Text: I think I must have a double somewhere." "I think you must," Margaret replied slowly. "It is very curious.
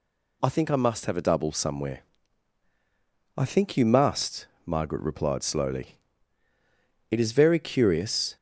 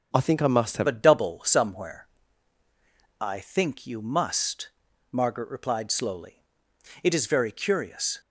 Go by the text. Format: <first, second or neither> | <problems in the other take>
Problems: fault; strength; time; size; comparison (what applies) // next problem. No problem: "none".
first | starts louder than the rest; strong; until 1.1 s; 7 dB // changes voice at "a"; from 0.8 s on; 7.4 s long